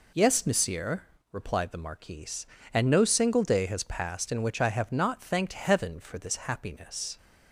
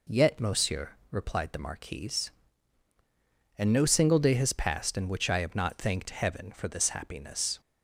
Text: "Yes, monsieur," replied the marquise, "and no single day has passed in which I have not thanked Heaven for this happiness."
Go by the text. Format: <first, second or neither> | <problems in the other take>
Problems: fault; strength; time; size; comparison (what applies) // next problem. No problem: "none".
first | says "Yet" for "Yes"; at 0.0 s